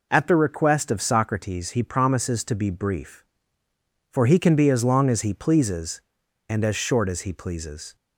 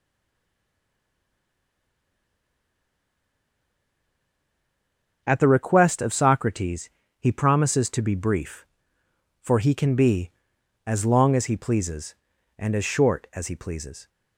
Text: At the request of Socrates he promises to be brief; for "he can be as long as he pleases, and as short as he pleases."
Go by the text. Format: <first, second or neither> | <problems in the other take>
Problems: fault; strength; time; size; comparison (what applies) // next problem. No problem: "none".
first | stays silent before the first word; strong; until 5.2 s; 5.2 s long // pauses between "Socrates" and "he"; slight; at 6.8 s; 0.32 s long